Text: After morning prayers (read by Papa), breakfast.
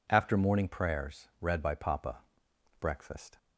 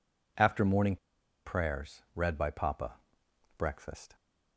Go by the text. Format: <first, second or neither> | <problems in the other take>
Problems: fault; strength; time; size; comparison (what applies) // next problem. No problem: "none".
first | pauses between "morning" and "prayers"; noticeable; at 0.9 s; 0.49 s long